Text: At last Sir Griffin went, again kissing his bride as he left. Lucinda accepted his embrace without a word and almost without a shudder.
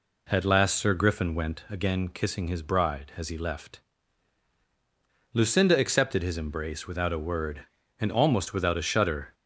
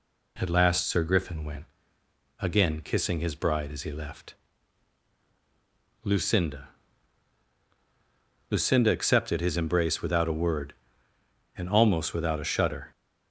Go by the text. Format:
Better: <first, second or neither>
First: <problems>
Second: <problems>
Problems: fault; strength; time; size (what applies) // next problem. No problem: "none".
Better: first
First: none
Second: says "Lucinda" twice; at 8.5 s